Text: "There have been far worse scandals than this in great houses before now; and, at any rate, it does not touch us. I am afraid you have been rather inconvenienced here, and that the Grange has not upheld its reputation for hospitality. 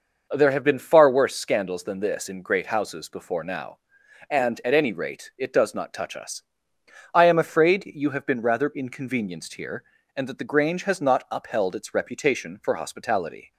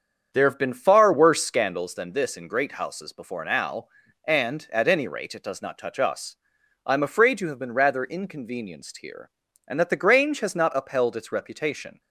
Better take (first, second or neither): first